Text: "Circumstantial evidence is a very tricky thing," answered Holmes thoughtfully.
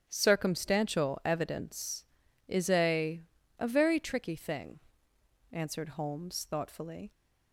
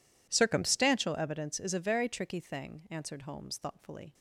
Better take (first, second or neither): second